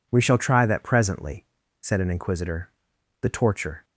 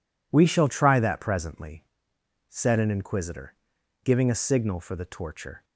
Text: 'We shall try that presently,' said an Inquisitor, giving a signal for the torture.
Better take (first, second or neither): second